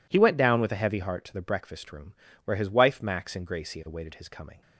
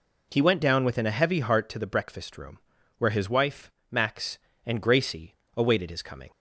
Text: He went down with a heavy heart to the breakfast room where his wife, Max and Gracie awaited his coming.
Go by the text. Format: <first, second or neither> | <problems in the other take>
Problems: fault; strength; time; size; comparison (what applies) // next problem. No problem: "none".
first | says "within" for "with"; at 0.8 s // pauses between "room" and "where"; at 2.5 s; 0.40 s long; slight in the first // pauses between "Gracie" and "awaited"; slight; at 5.3 s; 0.22 s long